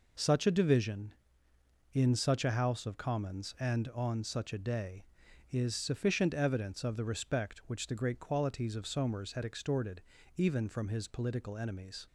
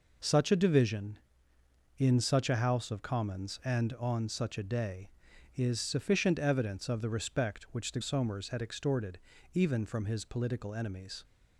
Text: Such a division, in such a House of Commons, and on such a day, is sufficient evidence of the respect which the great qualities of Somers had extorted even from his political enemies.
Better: first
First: pauses between "extorted" and "even"; slight; at 10.0 s; 0.34 s long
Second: skips "great qualities of"; at 8.0 s // pauses between "extorted" and "even"; slight; at 9.1 s; 0.34 s long

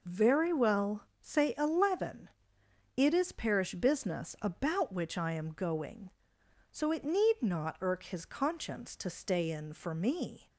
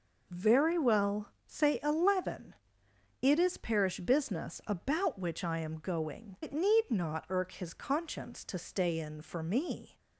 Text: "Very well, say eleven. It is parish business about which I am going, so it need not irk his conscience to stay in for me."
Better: first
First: none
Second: skips "so"; at 6.3 s

